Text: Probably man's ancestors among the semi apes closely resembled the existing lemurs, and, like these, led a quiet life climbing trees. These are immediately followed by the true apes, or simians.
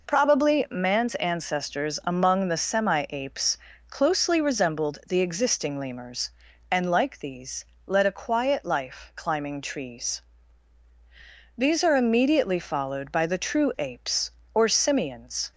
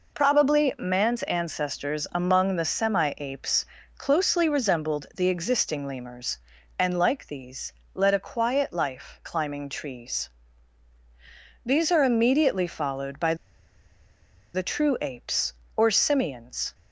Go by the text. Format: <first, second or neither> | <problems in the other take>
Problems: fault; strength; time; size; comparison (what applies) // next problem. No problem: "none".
first | pauses between "apes" and "closely"; slight; at 3.6 s; 0.36 s long; slight in the first // pauses between "by" and "the"; at 13.3 s; 1.1 s long